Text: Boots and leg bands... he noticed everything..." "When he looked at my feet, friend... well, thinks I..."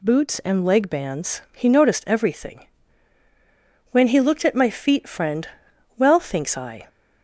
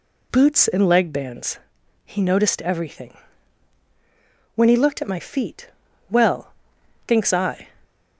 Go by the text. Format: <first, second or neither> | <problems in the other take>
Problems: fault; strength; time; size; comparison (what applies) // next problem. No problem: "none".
first | skips "friend"; at 5.8 s